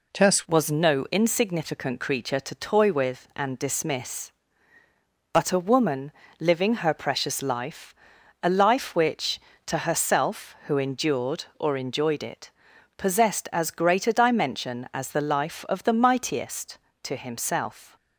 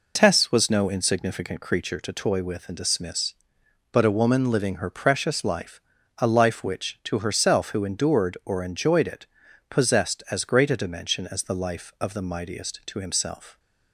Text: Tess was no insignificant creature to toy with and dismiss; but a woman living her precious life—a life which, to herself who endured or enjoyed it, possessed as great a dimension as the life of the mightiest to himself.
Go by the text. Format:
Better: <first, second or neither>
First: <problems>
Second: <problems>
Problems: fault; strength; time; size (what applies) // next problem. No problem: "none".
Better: second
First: changes voice at "was"; from 0.4 s on; 17.5 s long // pauses between "woman" and "living"; slight; at 6.1 s; 0.28 s long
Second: none